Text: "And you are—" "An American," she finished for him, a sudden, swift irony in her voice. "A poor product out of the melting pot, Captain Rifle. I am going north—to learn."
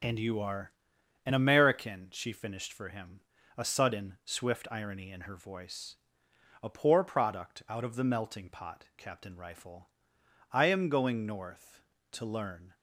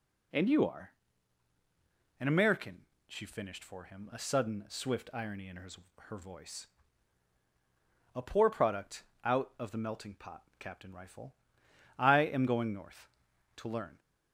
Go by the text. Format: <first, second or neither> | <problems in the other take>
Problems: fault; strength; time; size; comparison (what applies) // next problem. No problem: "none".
first | says "her" twice; at 6.0 s // pauses between "product" and "out"; slight; at 9.0 s; 0.22 s long